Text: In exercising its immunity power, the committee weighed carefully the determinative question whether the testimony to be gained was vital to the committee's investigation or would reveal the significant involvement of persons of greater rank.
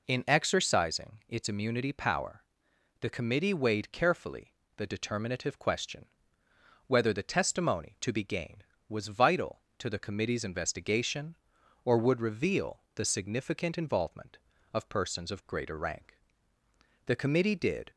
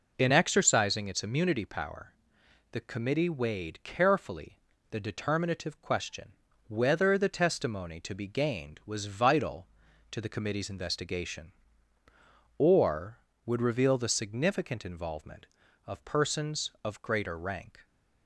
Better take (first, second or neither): second